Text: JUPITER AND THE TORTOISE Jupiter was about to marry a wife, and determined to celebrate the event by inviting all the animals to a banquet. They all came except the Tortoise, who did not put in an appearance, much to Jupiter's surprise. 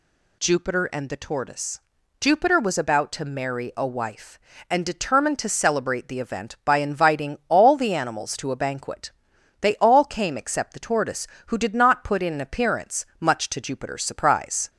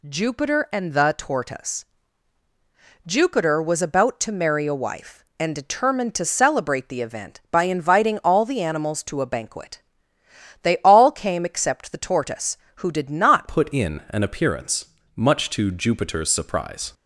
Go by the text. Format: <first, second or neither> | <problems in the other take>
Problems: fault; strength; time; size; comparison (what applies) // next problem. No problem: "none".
first | pauses between "TORTOISE" and "Jupiter"; at 1.8 s; 1.2 s long; also in the first // changes voice at "put"; from 13.4 s on; 3.5 s long